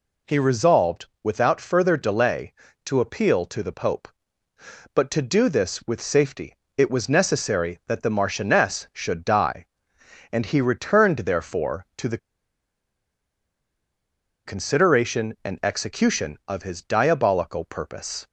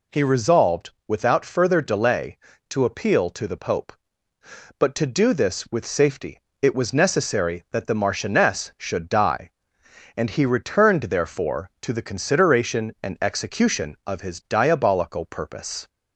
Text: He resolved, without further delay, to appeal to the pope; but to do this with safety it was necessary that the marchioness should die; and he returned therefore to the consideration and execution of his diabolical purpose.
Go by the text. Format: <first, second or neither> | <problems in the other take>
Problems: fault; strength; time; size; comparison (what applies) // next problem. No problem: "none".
second | pauses between "safety" and "it"; slight; at 6.5 s; 0.22 s long; slight in the second // pauses between "the" and "consideration"; strong; at 12.1 s; 2.2 s long